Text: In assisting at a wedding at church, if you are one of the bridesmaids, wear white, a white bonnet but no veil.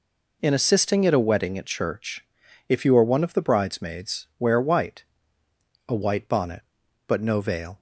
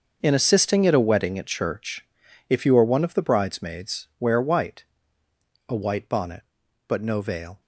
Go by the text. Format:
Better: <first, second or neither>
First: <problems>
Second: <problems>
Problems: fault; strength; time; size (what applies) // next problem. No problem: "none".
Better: first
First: none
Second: gets quieter; strong; throughout; 14 dB